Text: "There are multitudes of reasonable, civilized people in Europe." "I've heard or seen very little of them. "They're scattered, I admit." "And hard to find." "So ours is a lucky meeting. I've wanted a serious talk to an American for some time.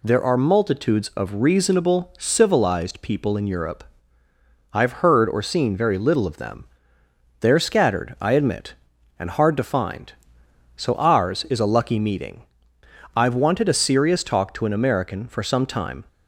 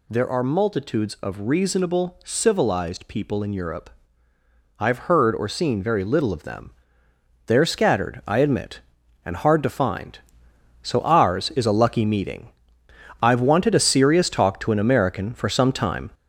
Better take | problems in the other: first | gets louder; noticeable; throughout; 5 dB

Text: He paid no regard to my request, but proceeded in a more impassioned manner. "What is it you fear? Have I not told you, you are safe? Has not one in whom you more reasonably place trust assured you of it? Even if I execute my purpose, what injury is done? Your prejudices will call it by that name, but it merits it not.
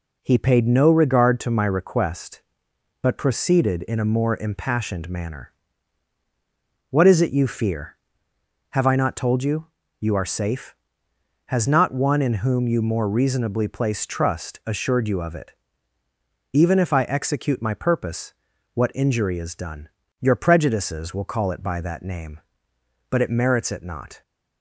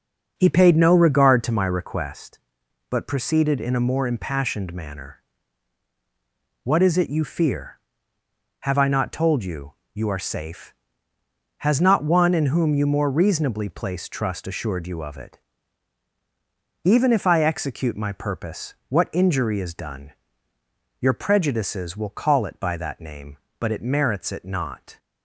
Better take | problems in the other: first | starts louder than the rest; until 2.2 s; 6.5 dB

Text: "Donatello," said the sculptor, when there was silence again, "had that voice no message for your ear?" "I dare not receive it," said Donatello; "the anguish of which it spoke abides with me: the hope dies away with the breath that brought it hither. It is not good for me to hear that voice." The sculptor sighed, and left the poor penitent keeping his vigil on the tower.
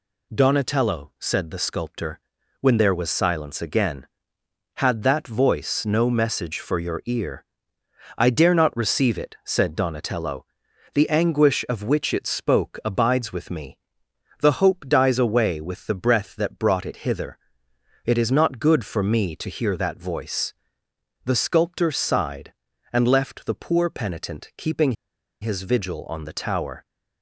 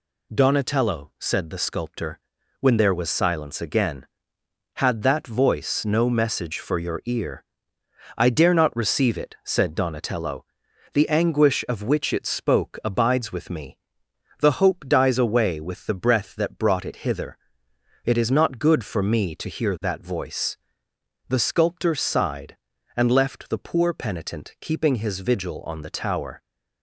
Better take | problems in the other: second | pauses between "keeping" and "his"; noticeable; at 24.9 s; 0.49 s long

